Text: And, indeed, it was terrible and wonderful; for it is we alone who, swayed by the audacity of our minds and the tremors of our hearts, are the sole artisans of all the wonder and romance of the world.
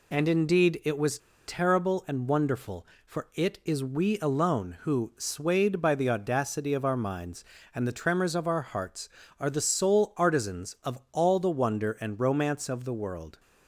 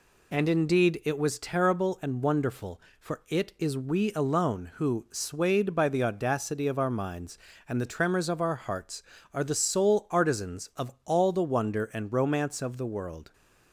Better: second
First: pauses between "was" and "terrible"; slight; at 1.1 s; 0.28 s long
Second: none

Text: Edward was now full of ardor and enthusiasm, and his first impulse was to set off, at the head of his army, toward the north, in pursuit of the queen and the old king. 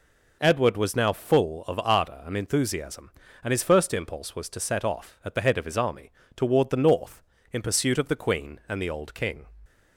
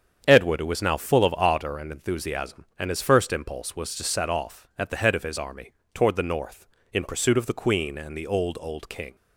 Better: first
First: none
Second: starts louder than the rest; strong; until 1.2 s; 8 dB // says "old" twice; at 8.5 s

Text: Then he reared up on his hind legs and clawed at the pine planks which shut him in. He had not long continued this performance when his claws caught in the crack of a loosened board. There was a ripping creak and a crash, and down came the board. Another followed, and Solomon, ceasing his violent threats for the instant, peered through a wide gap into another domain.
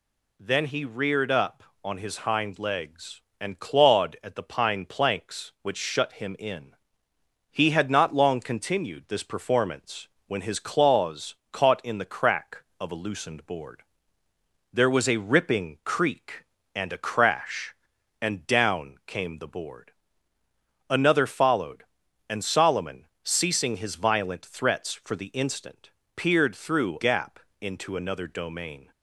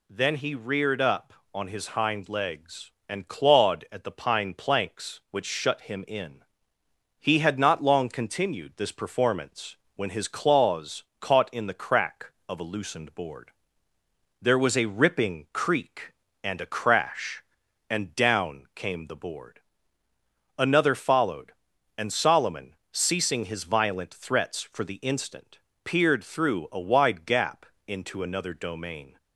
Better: second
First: pauses between "performance" and "when"; slight; at 10.0 s; 0.18 s long // pauses between "claws" and "caught"; slight; at 11.3 s; 0.16 s long // skips "a wide"; at 26.9 s // pauses between "gap" and "into"; slight; at 27.3 s; 0.22 s long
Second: pauses between "performance" and "when"; slight; at 9.7 s; 0.18 s long // pauses between "claws" and "caught"; slight; at 11.0 s; 0.16 s long // pauses between "gap" and "into"; slight; at 27.6 s; 0.22 s long

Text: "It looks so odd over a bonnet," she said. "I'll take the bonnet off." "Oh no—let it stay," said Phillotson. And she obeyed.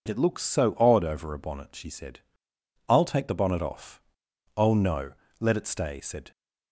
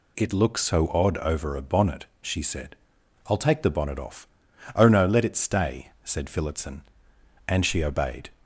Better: second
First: stops before "Phillotson And she obeyed"; at 6.3 s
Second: none

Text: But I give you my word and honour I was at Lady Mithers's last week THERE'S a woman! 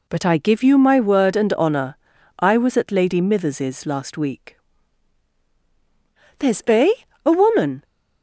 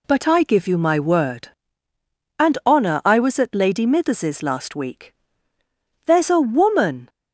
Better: second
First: pauses between "honour" and "I"; at 1.9 s; 0.44 s long // pauses between "week" and "THERE'S"; strong; at 4.5 s; 1.8 s long // says "a" twice; at 7.2 s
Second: pauses between "week" and "THERE'S"; noticeable; at 5.1 s; 0.92 s long

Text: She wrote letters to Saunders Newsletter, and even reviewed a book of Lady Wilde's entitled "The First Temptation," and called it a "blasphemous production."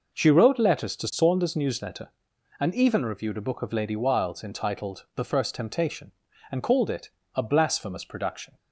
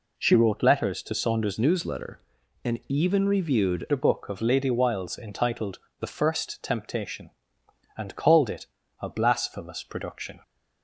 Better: first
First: pauses between "it" and "a"; slight; at 7.0 s; 0.24 s long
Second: changes voice from "Newsletter" to "reviewed"; from 1.5 to 3.8 s; 2.3 s long // pauses between "entitled" and "The"; slight; at 5.7 s; 0.20 s long // pauses between "it" and "a"; slight; at 8.6 s; 0.34 s long

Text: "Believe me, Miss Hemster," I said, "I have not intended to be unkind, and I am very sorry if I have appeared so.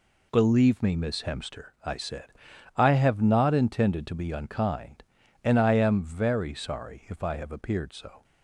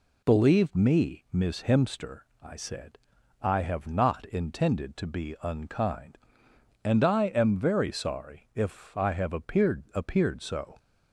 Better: first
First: none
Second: says "appeared" twice; at 9.9 s

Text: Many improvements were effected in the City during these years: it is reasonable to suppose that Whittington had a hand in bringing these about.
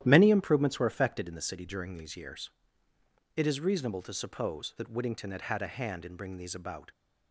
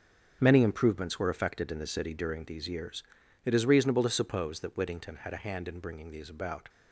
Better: second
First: starts louder than the rest; strong; until 1.0 s; 12 dB // says "had" twice; at 5.4 s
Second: starts louder than the rest; strong; until 1.4 s; 7.5 dB

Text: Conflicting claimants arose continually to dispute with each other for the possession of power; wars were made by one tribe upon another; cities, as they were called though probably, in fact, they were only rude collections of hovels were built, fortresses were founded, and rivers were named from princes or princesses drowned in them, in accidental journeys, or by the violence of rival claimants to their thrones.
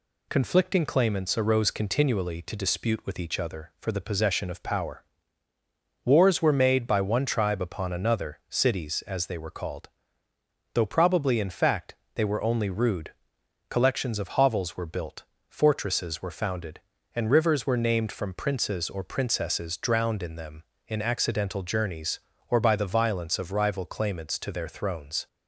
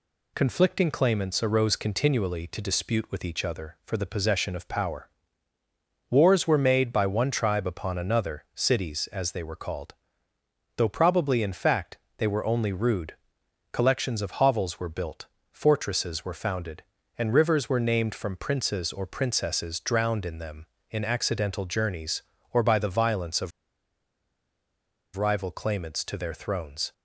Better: first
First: pauses between "called" and "though"; noticeable; at 9.8 s; 0.84 s long // pauses between "rude" and "collections"; noticeable; at 13.1 s; 0.58 s long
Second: pauses between "called" and "though"; noticeable; at 9.9 s; 0.82 s long // pauses between "rude" and "collections"; noticeable; at 13.1 s; 0.58 s long // pauses between "of" and "rival"; strong; at 23.5 s; 1.6 s long

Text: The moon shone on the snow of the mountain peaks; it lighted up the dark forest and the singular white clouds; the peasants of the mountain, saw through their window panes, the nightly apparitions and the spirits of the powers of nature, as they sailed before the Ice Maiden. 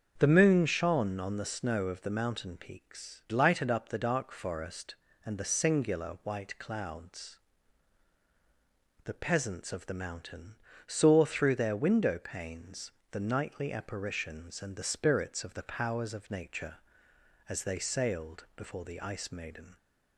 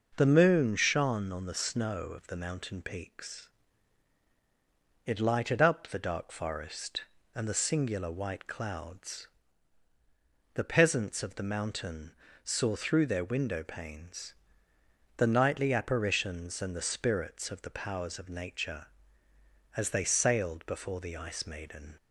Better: second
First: starts louder than the rest; until 1.1 s; 6.5 dB // skips "it"; at 3.2 s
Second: none

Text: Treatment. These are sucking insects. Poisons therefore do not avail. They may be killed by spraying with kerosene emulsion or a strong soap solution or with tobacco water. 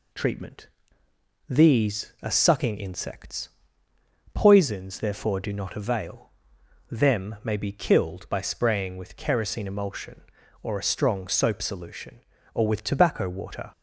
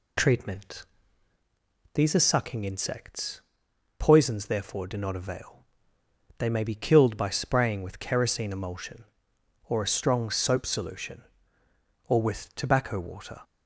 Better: second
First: says "Them" for "They"; at 6.8 s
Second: none

